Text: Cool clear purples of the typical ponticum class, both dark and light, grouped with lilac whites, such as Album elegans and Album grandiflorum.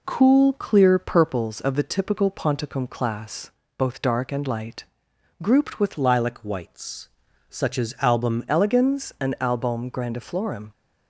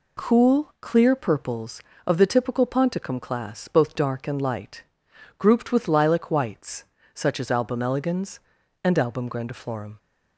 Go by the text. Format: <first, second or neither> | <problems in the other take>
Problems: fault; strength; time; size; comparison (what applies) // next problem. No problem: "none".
second | changes voice from "lilac" to "Album"; from 5.9 to 8.4 s; 2.5 s long